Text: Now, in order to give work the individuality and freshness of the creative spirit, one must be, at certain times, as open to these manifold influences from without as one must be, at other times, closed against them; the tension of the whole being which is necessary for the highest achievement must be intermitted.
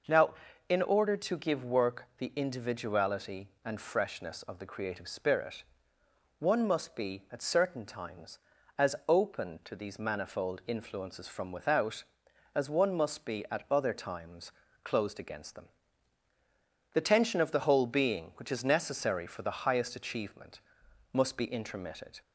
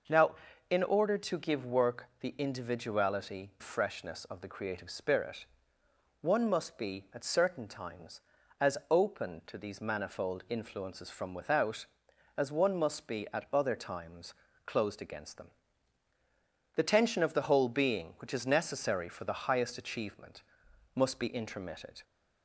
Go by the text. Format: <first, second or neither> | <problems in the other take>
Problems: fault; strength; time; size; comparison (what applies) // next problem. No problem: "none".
first | pauses between "work" and "the"; slight; at 2.0 s; 0.16 s long // skips "and"; at 3.5 s // pauses between "achievement" and "must"; noticeable; at 20.4 s; 0.52 s long; noticeable in the first